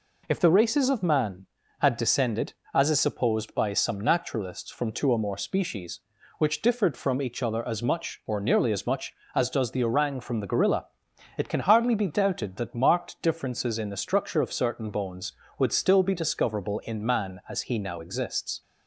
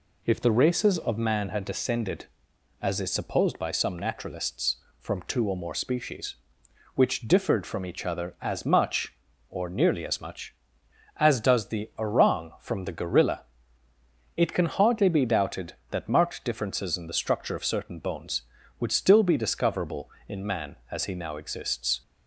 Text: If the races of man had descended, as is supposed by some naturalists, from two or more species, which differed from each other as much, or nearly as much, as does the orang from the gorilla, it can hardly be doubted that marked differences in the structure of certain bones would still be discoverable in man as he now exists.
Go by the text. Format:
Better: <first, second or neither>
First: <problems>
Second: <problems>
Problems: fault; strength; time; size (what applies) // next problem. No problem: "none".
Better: neither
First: none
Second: none